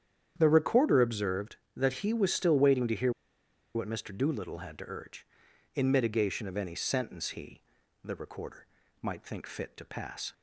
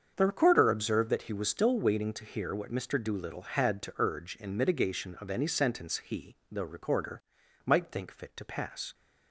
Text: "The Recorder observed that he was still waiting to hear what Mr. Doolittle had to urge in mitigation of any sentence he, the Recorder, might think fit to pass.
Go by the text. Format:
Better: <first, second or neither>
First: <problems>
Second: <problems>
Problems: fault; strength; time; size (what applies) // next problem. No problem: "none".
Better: second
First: starts louder than the rest; strong; until 1.3 s; 9 dB // pauses between "hear" and "what"; noticeable; at 3.1 s; 0.64 s long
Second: starts louder than the rest; strong; until 1.1 s; 7 dB